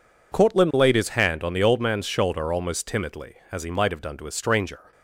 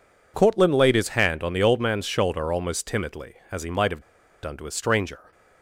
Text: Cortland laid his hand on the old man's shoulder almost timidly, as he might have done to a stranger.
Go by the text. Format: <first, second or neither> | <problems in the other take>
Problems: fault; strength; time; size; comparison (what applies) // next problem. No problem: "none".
first | pauses between "have" and "done"; at 4.0 s; 0.41 s long